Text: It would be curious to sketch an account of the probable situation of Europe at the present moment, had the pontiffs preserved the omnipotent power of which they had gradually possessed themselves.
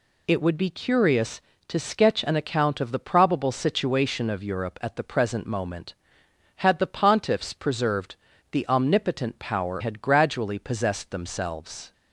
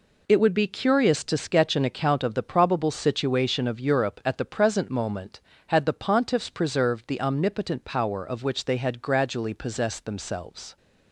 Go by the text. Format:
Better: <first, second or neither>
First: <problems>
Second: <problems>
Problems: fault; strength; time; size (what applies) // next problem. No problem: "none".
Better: second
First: pauses between "preserved" and "the"; at 8.1 s; 0.38 s long // skips "of which they"; at 9.7 s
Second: none